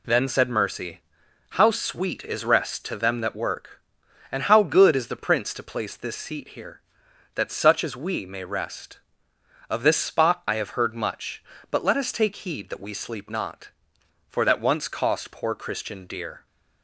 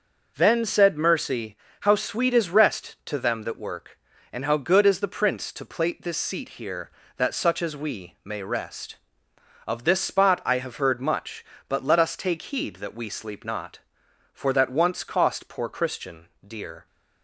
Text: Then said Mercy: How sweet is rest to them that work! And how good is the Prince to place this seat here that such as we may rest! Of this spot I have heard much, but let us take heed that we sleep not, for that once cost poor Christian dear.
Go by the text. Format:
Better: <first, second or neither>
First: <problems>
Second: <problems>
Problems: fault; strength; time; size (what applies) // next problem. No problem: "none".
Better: first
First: none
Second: says "plate" for "place"; at 5.6 s // pauses between "Christian" and "dear"; slight; at 16.2 s; 0.18 s long